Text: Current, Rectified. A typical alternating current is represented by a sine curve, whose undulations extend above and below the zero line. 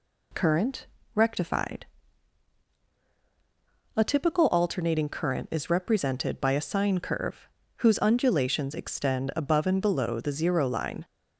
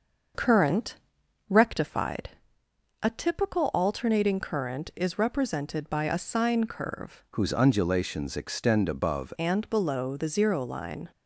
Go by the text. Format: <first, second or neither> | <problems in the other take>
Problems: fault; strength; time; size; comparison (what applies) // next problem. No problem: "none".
first | starts louder than the rest; noticeable; until 1.8 s; 6 dB // changes voice from "whose" to "above"; from 7.3 to 9.3 s; 2.0 s long